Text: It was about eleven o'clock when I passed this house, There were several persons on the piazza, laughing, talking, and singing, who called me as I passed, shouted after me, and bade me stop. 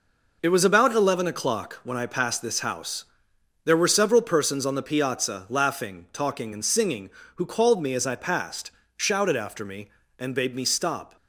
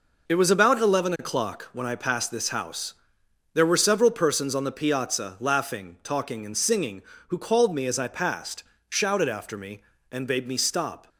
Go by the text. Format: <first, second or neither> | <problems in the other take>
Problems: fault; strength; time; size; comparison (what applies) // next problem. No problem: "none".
neither | none